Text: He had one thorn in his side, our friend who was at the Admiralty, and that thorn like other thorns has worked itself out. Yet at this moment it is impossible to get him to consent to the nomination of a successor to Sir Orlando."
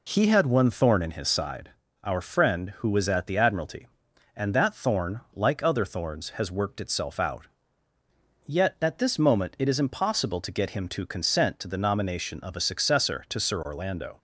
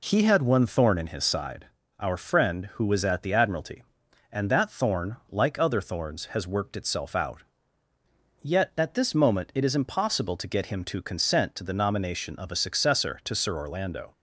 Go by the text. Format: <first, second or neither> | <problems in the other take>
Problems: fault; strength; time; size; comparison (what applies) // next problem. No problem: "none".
neither | none